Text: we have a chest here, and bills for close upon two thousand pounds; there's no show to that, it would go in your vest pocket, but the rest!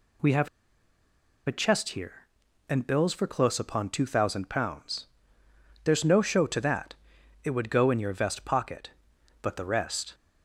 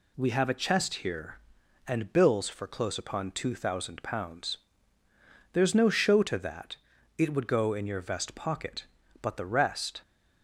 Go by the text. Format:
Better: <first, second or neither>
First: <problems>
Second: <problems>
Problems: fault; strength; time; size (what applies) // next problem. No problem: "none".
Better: second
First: pauses between "have" and "a"; at 0.4 s; 0.99 s long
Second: none